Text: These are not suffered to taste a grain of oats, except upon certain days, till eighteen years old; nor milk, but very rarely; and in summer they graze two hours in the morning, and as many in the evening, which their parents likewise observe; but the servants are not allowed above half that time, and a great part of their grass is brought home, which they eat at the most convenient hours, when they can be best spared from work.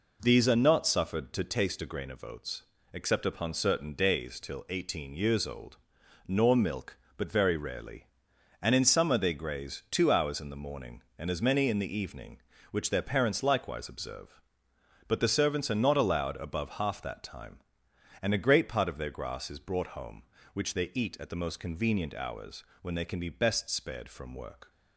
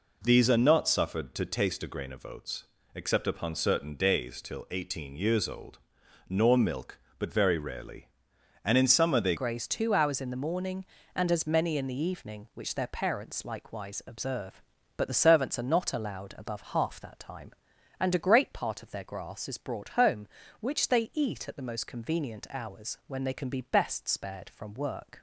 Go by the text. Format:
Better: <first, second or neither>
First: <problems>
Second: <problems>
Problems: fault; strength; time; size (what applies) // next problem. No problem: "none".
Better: first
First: none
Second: changes voice at "graze"; from 9.3 s on; 15.9 s long